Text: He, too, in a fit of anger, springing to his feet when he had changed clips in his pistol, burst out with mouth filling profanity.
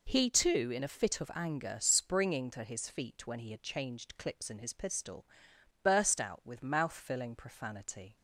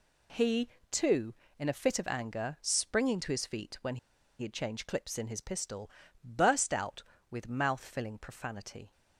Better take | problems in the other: first | pauses between "when" and "he"; at 3.9 s; 0.42 s long

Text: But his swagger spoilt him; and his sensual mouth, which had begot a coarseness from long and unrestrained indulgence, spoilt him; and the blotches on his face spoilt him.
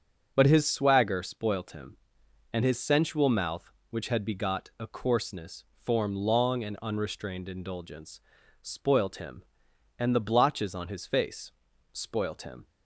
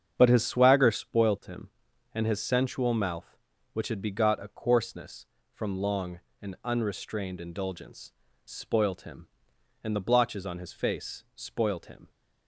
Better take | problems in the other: second | starts louder than the rest; strong; until 1.3 s; 7.5 dB; strong in the second // says "form" for "from"; at 5.7 s // pauses between "face" and "spoilt"; at 11.5 s; 0.40 s long

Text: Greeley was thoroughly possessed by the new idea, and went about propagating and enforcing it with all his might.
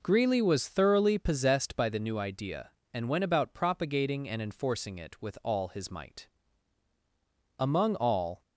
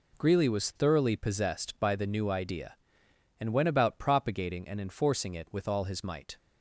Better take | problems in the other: second | goes on to say "Among all"; noticeable; from 7.5 s on; 0.84 s long

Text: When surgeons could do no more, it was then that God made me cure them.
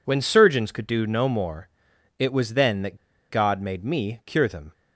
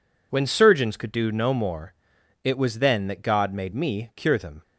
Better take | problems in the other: second | pauses between "that" and "God"; slight; at 2.9 s; 0.32 s long

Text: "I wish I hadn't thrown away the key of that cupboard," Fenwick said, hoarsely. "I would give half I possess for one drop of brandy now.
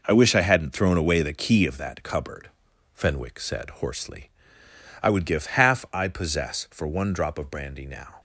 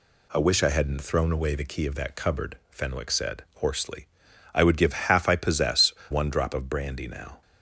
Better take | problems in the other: first | skips "for"; at 6.0 s

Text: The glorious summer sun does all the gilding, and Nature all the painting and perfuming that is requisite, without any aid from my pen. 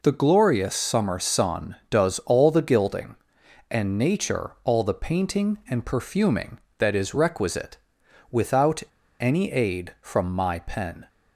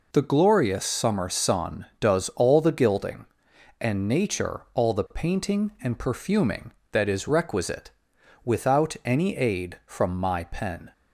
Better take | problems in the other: second | pauses between "without" and "any"; at 8.8 s; 0.38 s long

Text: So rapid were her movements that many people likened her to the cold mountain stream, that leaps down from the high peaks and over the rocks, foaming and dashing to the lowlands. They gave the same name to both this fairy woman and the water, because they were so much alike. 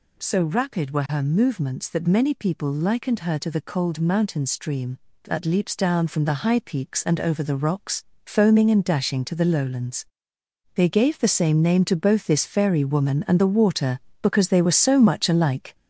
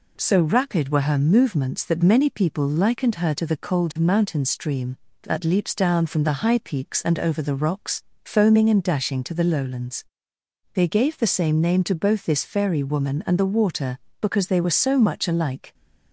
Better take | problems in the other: second | gets louder; noticeable; throughout; 6 dB

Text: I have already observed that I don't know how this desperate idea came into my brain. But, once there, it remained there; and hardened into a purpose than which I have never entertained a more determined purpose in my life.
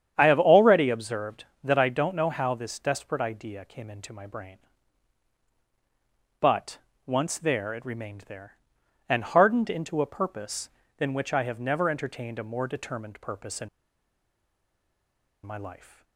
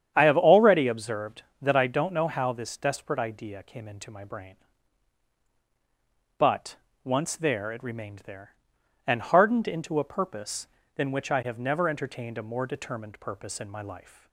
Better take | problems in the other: second | starts louder than the rest; strong; until 1.1 s; 9 dB; strong in the second // pauses between "in" and "my"; strong; at 13.6 s; 1.7 s long

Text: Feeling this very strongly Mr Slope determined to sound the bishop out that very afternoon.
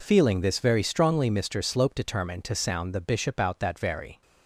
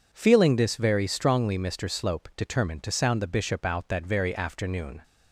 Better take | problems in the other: second | stops before "afternoon"; at 4.2 s

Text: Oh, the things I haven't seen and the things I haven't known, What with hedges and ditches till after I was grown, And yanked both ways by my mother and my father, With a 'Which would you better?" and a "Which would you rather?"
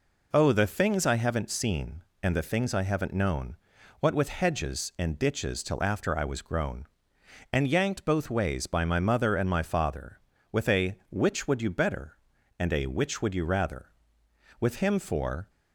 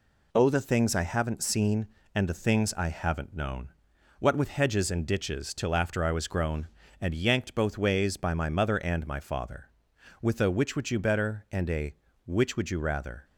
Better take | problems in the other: second | goes on to say "With him for"; noticeable; from 14.6 s on; 0.88 s long

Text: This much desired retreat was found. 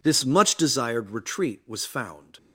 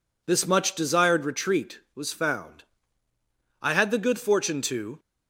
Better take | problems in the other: first | goes on to say "I had the good fortune to"; from 3.6 s on; 1.3 s long

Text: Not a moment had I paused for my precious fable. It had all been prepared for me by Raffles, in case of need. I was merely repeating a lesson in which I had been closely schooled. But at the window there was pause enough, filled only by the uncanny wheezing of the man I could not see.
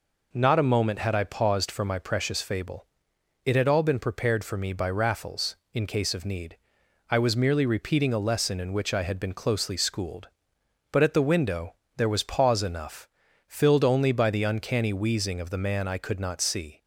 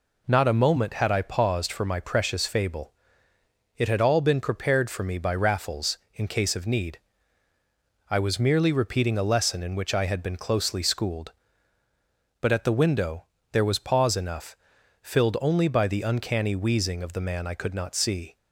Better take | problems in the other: neither | pauses between "window" and "there"; slight; the same in both

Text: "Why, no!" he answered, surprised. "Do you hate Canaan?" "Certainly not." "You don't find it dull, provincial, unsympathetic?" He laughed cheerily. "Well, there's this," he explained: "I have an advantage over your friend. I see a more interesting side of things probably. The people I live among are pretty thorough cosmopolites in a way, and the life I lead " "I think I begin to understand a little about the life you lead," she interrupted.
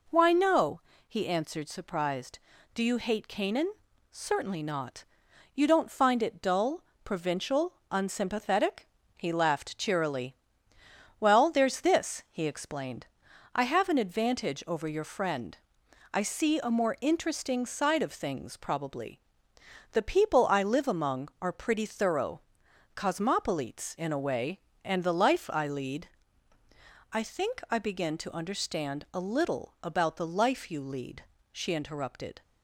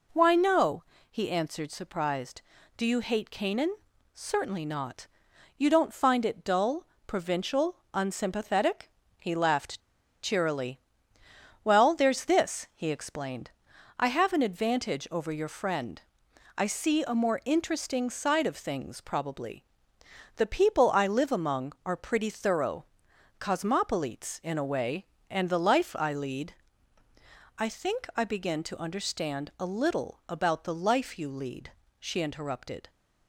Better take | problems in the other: first | pauses between "laughed" and "cheerily"; at 9.7 s; 0.42 s long // pauses between "thorough" and "cosmopolites"; noticeable; at 22.8 s; 0.54 s long; noticeable in the first

